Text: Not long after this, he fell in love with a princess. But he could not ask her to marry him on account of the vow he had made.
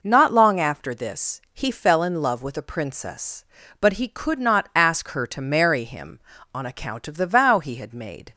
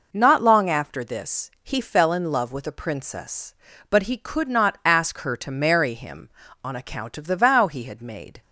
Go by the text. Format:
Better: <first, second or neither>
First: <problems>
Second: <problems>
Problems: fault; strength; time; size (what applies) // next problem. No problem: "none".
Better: neither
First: none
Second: none